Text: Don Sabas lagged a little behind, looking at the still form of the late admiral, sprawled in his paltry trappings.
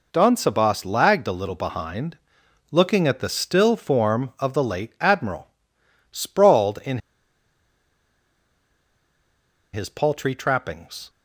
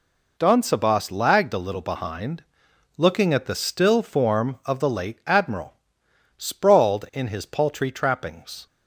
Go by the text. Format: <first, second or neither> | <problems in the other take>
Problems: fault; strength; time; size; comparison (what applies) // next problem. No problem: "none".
second | pauses between "in" and "his"; strong; at 6.9 s; 2.7 s long